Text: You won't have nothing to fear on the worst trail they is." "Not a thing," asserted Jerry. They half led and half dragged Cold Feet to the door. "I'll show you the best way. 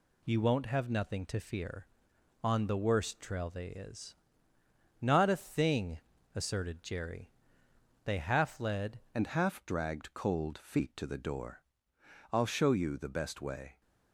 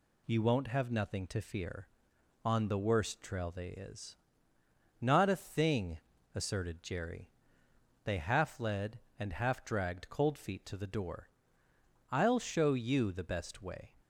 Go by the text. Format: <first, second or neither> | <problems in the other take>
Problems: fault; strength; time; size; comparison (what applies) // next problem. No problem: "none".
second | changes voice at "and"; from 9.1 s on; 4.7 s long